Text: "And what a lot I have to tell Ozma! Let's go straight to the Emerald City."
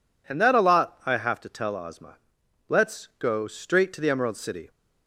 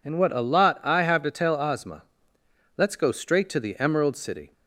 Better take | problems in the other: second | says "that" for "what"; at 0.4 s

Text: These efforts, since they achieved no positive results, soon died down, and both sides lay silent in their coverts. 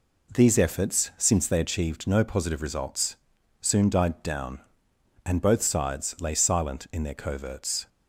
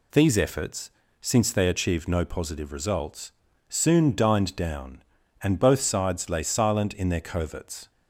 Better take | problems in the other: first | says "dined" for "died"; at 4.1 s

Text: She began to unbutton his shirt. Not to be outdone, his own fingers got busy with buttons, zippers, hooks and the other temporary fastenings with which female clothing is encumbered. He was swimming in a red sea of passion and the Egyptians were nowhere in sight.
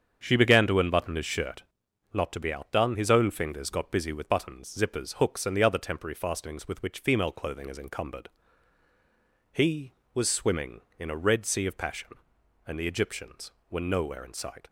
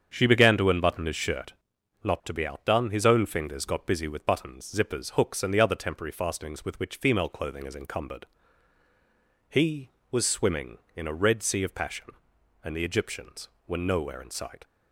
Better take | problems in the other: neither | starts louder than the rest; strong; the same in both

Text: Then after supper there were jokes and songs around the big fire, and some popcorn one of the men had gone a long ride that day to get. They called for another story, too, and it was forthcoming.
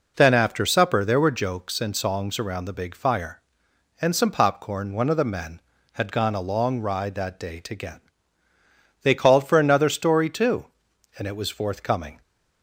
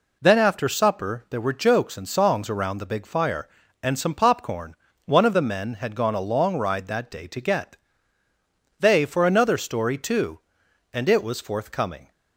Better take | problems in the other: first | pauses between "popcorn" and "one"; slight; at 4.7 s; 0.30 s long // skips "called"; at 9.0 s

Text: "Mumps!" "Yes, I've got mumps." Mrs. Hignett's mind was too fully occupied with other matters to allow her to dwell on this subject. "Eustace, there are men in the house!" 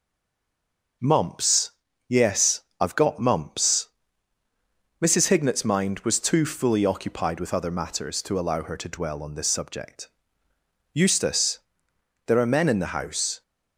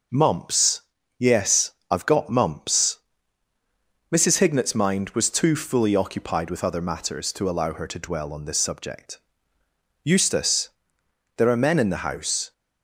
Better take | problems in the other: second | stays silent before the first word; until 1.0 s; 1.0 s long

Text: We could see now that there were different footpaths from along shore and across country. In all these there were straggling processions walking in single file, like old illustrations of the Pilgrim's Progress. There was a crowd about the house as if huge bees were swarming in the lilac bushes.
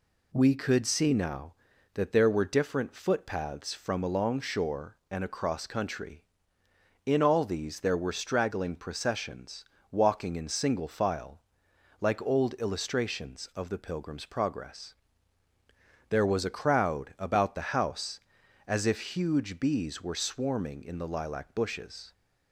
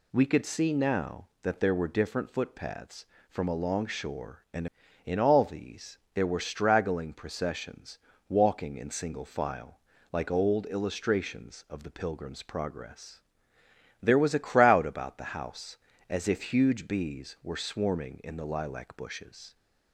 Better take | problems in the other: first | skips "across country"; at 4.8 s // pauses between "these" and "there"; slight; at 5.9 s; 0.16 s long // pauses between "processions" and "walking"; slight; at 7.9 s; 0.30 s long; slight in the first

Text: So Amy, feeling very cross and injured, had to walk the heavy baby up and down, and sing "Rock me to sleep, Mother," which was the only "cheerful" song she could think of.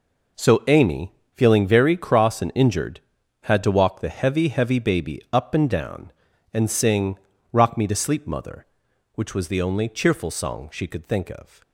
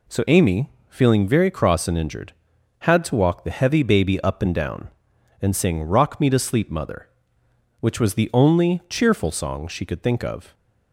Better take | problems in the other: second | says "heavy" twice; at 4.4 s // pauses between "sing" and "Rock"; slight; at 7.1 s; 0.34 s long

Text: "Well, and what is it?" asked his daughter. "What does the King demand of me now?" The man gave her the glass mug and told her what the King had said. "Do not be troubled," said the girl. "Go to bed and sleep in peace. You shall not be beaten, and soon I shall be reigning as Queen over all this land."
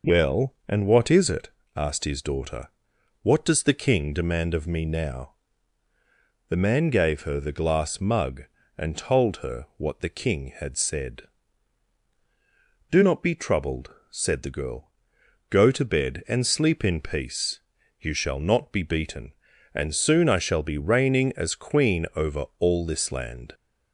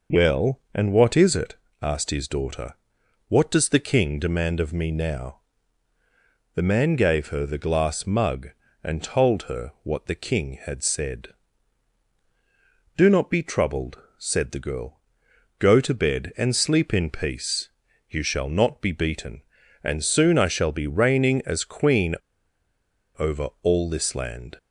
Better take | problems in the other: first | pauses between "Queen" and "over"; at 22.1 s; 1.0 s long

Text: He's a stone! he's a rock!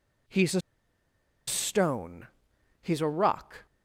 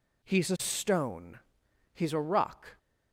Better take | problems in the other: second | pauses between "a" and "stone"; noticeable; at 0.6 s; 0.86 s long

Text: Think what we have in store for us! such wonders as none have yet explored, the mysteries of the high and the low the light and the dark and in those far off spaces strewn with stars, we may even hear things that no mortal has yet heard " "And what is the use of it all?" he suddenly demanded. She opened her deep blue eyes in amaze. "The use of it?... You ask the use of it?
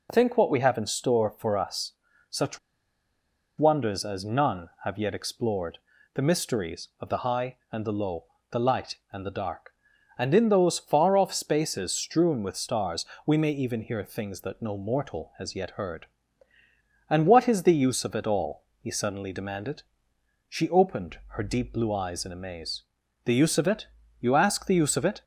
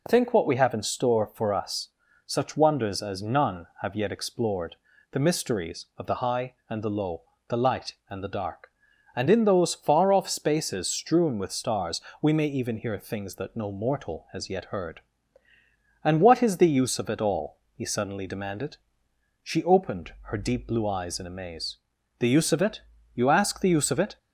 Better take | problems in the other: second | pauses between "such" and "wonders"; at 2.5 s; 1.0 s long // pauses between "low" and "the"; slight; at 8.2 s; 0.26 s long; slight in the second

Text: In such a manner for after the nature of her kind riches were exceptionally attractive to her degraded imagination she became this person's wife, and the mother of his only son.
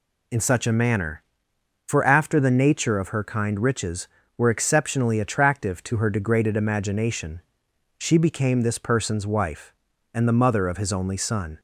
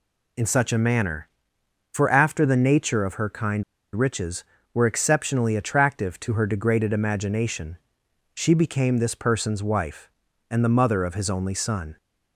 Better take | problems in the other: first | pauses between "kind" and "riches"; slight; at 3.6 s; 0.31 s long // pauses between "imagination" and "she"; noticeable; at 7.7 s; 0.58 s long; noticeable in the first

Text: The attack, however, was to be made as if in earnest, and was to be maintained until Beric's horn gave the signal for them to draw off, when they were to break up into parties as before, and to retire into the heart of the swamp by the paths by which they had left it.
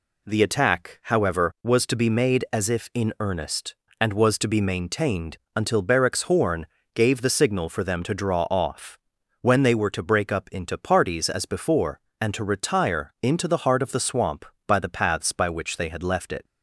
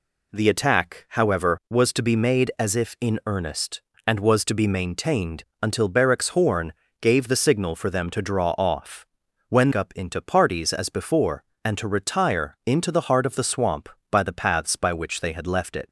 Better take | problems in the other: first | pauses between "maintained" and "until"; slight; at 5.4 s; 0.18 s long; slight in the first // pauses between "horn" and "gave"; slight; at 6.7 s; 0.26 s long; slight in the first // skips "they were to break"; at 9.7 s

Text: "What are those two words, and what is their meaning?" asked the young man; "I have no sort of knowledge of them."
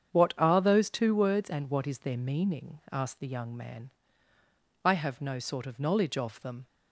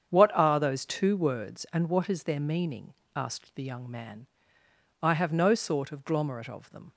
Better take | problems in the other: first | starts louder than the rest; strong; until 1.1 s; 8 dB; strong in the first // says "glomerate" for "knowledge"; at 6.0 s

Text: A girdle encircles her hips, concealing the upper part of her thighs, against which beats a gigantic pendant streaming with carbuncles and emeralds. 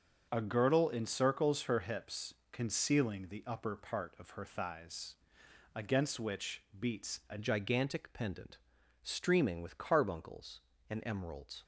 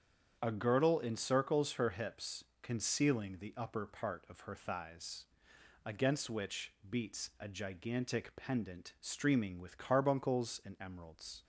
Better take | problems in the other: second | starts louder than the rest; until 1.3 s; 6.5 dB; strong in the second // pauses between "which" and "beats"; slight; at 6.6 s; 0.16 s long; slight in the second // changes voice at "gigantic"; from 7.3 s on; 4.3 s long // pauses between "pendant" and "streaming"; at 8.5 s; 0.42 s long

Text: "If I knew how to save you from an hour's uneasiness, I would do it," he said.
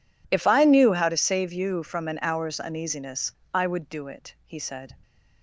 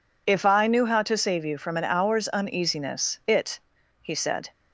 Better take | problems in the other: first | skips "I would do"; at 3.2 s

